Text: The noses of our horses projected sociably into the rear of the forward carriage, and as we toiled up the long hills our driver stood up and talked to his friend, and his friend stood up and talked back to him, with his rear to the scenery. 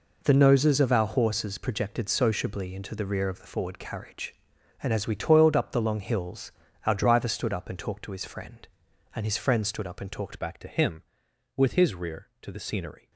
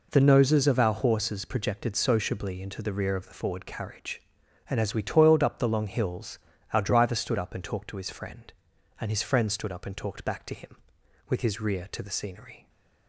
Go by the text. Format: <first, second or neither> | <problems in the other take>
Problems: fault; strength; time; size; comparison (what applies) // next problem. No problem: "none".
second | pauses between "hills" and "our"; slight; at 6.5 s; 0.34 s long; slight in the second // changes voice at "back"; from 10.3 s on; 2.8 s long